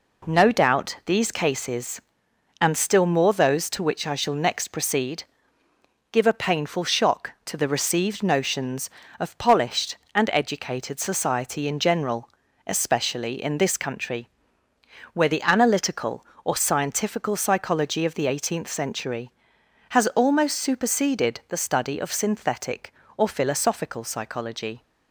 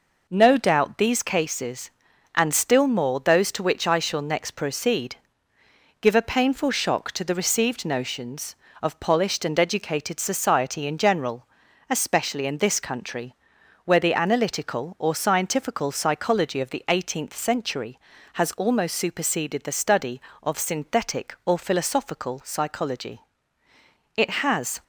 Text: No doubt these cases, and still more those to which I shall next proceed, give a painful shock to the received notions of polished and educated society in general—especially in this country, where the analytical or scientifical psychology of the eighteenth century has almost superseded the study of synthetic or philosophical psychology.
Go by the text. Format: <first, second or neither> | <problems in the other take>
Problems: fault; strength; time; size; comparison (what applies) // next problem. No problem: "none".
first | goes on to say "It has"; noticeable; from 24.1 s on; 0.68 s long